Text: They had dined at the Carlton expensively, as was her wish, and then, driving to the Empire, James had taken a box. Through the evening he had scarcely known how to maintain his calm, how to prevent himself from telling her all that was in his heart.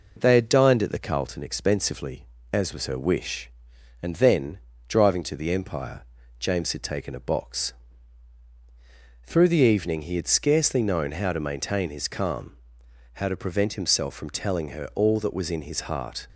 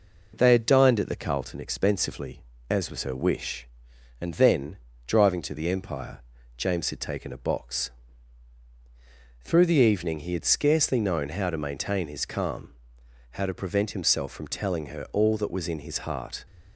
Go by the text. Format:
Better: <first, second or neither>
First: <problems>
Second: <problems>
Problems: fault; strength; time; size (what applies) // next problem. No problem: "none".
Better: neither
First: none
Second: none